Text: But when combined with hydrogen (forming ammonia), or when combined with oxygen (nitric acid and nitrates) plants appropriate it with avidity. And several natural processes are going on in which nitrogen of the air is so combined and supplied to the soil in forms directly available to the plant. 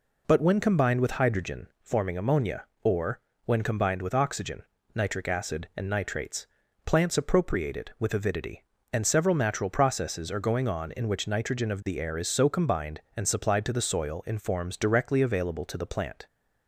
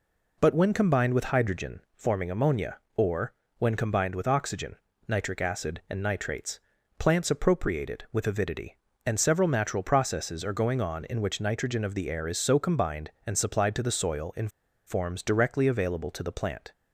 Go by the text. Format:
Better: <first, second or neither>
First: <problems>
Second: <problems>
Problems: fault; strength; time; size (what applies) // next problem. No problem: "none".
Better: first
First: pauses between "or" and "when"; slight; at 3.1 s; 0.26 s long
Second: pauses between "or" and "when"; slight; at 3.3 s; 0.26 s long // pauses between "in" and "forms"; at 14.4 s; 0.38 s long